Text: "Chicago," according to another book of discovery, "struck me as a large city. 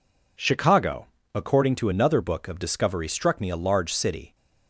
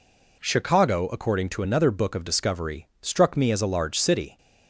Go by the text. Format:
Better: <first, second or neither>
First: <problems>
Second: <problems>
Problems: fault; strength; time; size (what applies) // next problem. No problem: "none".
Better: second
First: skips "as"; at 3.4 s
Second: none